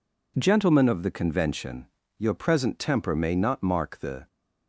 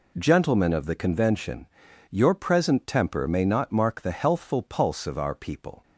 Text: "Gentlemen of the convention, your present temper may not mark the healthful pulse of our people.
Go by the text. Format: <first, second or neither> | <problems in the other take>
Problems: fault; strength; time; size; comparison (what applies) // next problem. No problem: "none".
second | stops before "healthful pulse of our people"; at 4.2 s